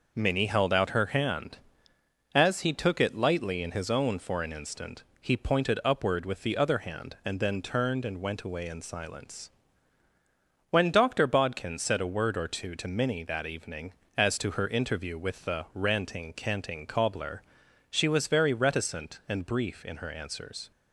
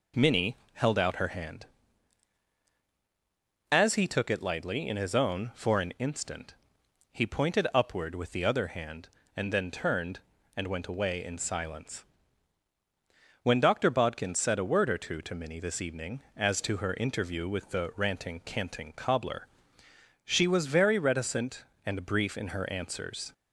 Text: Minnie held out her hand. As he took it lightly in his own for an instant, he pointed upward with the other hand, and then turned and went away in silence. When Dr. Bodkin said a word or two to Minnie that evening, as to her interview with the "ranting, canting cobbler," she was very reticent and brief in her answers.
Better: first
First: none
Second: pauses between "Minnie" and "held"; slight; at 0.5 s; 0.18 s long // says "this" for "that"; at 15.5 s

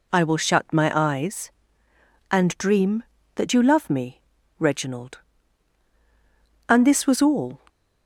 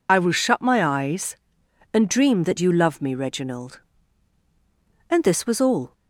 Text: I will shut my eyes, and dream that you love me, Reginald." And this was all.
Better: first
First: none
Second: loses the start of "I"; at 0.0 s; 55 ms

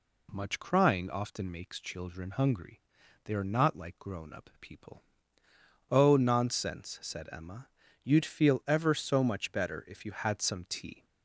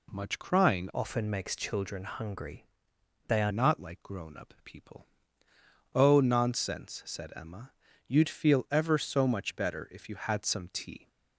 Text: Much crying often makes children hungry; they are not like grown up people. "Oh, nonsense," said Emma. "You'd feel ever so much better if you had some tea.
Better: first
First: none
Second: changes voice from "often" to "are"; from 0.9 to 3.5 s; 2.6 s long

